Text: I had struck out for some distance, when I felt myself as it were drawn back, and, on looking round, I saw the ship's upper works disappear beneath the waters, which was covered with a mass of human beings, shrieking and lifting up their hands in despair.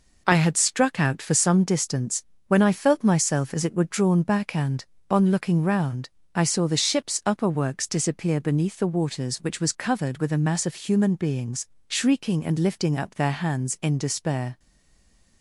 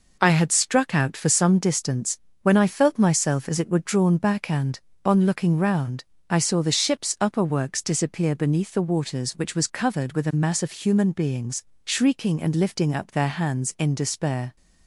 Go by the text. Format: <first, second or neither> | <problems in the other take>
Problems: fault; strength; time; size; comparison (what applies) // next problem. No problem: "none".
second | stays silent after the last word; slight; from 14.5 s on; 0.9 s long